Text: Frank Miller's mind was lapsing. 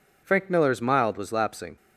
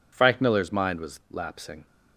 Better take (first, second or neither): second